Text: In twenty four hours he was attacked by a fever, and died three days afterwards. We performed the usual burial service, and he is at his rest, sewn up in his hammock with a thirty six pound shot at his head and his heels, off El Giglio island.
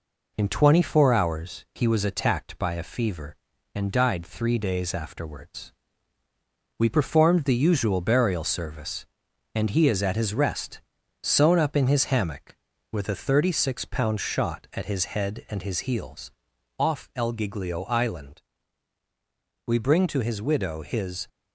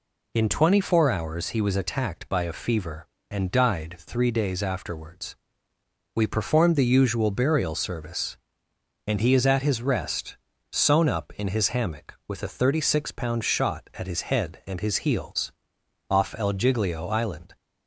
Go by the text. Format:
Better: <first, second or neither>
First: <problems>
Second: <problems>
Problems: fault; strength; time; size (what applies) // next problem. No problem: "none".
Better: second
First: goes on to say "We bring to his widow his"; from 19.6 s on; 1.6 s long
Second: none